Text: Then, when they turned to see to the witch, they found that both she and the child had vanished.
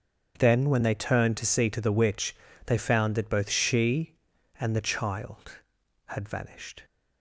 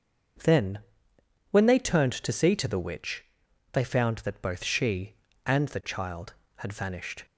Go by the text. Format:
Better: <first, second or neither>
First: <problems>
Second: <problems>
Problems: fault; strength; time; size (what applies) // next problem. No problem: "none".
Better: neither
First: starts louder than the rest; until 1.3 s; 7 dB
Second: starts louder than the rest; until 2.1 s; 6.5 dB